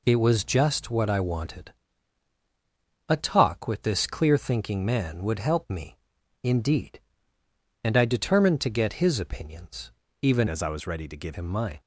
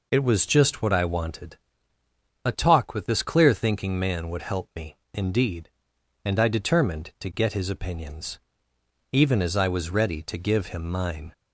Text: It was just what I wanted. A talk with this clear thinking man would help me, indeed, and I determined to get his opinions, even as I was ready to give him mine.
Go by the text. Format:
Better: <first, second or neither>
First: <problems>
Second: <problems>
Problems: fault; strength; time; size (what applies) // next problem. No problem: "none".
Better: second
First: changes voice from "as" to "give"; from 10.4 to 11.3 s; 0.9 s long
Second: none